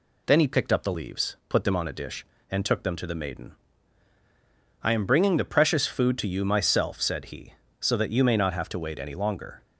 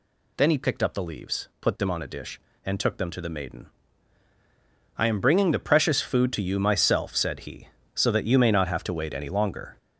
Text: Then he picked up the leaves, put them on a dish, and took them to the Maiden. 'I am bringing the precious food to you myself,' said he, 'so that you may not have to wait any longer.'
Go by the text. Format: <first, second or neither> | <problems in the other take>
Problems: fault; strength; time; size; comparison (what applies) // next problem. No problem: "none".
first | gets louder; throughout; 6.5 dB